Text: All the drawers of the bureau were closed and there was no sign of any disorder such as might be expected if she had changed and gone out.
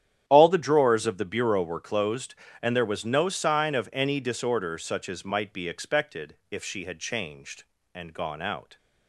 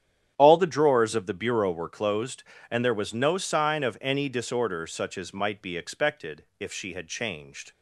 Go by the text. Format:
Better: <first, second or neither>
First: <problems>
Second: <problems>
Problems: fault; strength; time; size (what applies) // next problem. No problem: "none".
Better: first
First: starts louder than the rest; strong; until 1.2 s; 10 dB // pauses between "expected" and "if"; slight; at 6.3 s; 0.16 s long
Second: starts louder than the rest; strong; until 1.3 s; 10 dB // pauses between "expected" and "if"; slight; at 6.4 s; 0.16 s long // stops before "and gone out"; at 7.7 s